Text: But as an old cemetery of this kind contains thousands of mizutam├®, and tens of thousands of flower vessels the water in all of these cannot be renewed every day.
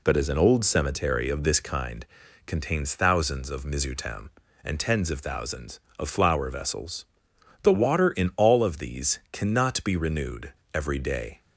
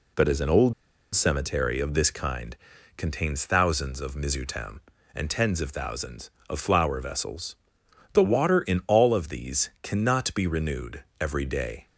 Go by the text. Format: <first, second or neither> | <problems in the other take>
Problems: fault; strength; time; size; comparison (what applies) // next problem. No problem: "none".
first | pauses between "old" and "cemetery"; at 0.7 s; 0.41 s long // pauses between "kind" and "contains"; at 2.5 s; 0.42 s long; also in the first // pauses between "vessels" and "the"; noticeable; at 7.5 s; 0.58 s long; noticeable in the first // pauses between "renewed" and "every"; slight; at 11.0 s; 0.16 s long; slight in the first